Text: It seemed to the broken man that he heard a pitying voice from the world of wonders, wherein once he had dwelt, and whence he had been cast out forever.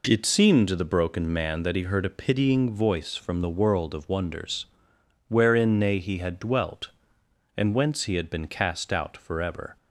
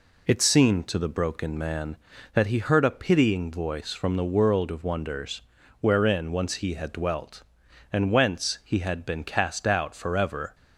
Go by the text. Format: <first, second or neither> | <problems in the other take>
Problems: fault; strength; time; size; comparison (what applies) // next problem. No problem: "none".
second | says "nay" for "once"; at 5.7 s